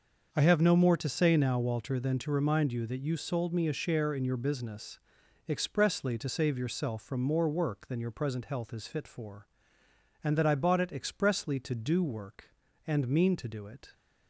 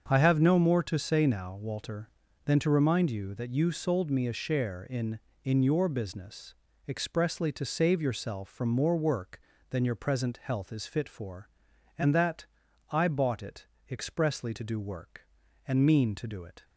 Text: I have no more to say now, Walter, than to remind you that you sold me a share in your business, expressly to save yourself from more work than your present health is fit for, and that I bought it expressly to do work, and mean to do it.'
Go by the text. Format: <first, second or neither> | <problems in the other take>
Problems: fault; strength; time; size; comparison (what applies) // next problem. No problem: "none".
first | starts louder than the rest; until 1.0 s; 6.5 dB; noticeable in the first // says "in" twice; at 5.4 s // pauses between "that" and "I"; noticeable; at 12.4 s; 0.46 s long // pauses between "it" and "expressly"; slight; at 13.6 s; 0.24 s long